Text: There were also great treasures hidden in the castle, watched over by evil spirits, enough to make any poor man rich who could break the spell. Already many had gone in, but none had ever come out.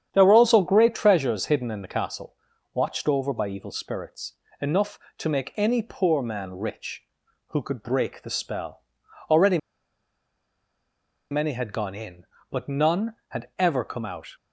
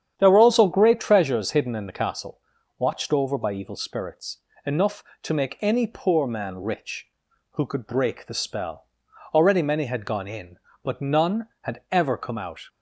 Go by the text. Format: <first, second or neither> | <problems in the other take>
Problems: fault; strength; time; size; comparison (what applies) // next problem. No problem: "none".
second | starts louder than the rest; strong; until 1.1 s; 9 dB; strong in the second // pauses between "Already" and "many"; strong; at 9.5 s; 1.7 s long